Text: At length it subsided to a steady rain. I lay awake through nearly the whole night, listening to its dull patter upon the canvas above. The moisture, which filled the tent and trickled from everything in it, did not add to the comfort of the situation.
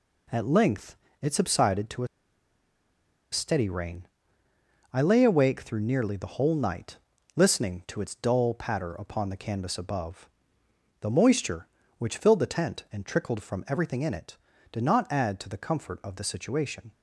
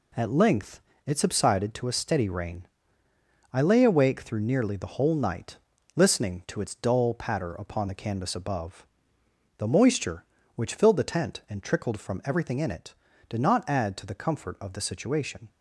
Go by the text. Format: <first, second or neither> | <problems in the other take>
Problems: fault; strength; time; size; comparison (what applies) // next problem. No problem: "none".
second | pauses between "length" and "it"; slight; at 0.9 s; 0.26 s long; slight in the second // pauses between "a" and "steady"; strong; at 2.0 s; 1.2 s long